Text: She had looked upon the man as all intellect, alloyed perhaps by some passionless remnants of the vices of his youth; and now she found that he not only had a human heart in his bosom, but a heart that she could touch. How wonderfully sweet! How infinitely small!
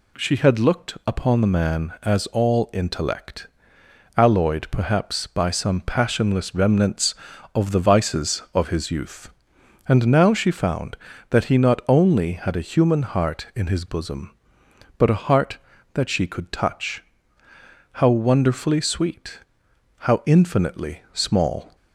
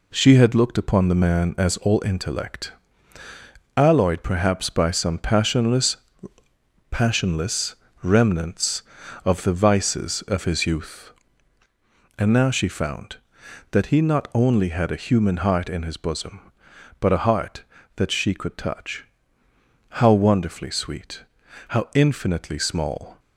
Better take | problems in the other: first | says "passionless" twice; at 6.8 s

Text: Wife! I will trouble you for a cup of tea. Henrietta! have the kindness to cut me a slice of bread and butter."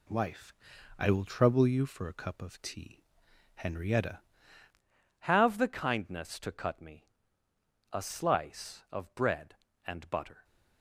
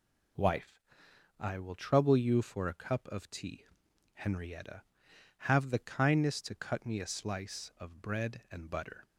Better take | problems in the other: second | changes voice at "have"; from 5.1 s on; 5.3 s long // pauses between "me" and "a"; noticeable; at 7.0 s; 0.86 s long

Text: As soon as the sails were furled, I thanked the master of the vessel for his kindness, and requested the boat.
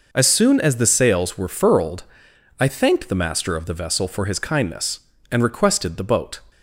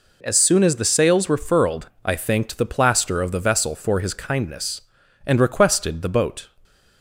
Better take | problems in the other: first | says "plaster" for "master"; at 2.6 s

